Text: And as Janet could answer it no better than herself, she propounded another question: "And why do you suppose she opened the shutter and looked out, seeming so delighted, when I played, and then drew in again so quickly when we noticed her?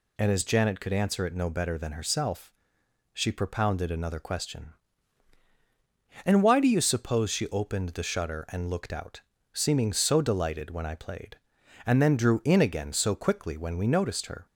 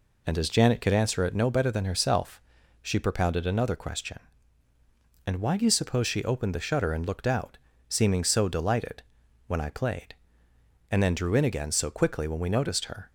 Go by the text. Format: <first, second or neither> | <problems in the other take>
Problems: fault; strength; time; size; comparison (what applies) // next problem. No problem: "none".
neither | none